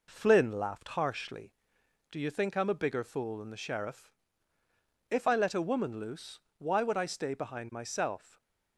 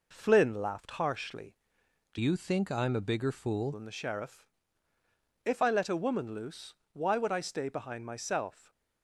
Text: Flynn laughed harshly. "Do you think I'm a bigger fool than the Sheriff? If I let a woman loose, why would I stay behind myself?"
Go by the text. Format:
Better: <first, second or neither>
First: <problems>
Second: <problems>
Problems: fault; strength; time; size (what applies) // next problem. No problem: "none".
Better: first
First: stays silent after the last word; slight; from 8.1 s on; 0.6 s long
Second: changes voice from "you" to "fool"; from 2.1 to 3.7 s; 1.6 s long // stays silent after the last word; slight; from 8.5 s on; 0.5 s long